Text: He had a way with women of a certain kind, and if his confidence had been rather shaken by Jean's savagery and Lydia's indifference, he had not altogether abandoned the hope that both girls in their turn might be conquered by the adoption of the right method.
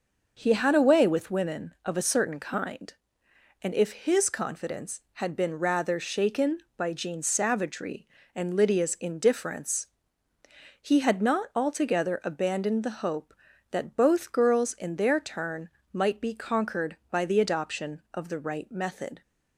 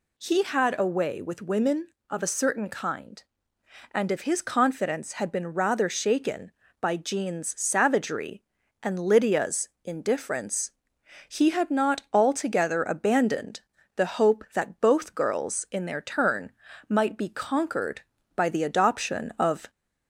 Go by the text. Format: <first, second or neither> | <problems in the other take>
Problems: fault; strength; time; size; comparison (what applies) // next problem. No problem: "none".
first | pauses between "Lydia's" and "indifference"; slight; at 9.6 s; 0.16 s long // pauses between "abandoned" and "the"; slight; at 13.6 s; 0.34 s long // pauses between "turn" and "might"; slight; at 16.5 s; 0.36 s long; slight in the first // stops before "the right method"; at 19.6 s